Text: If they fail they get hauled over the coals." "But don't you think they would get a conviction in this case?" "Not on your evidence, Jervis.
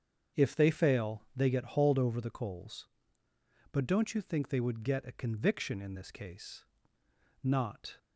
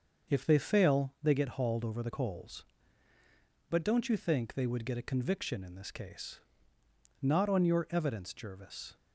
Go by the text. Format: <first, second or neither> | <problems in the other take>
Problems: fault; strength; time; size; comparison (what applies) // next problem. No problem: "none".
second | starts louder than the rest; strong; until 1.4 s; 7 dB; also in the second // stops before "on your evidence Jervis"; at 7.9 s